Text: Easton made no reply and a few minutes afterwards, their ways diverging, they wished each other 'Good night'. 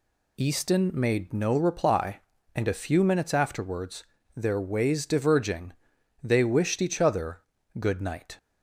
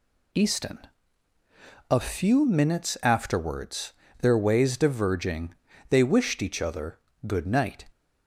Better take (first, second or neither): first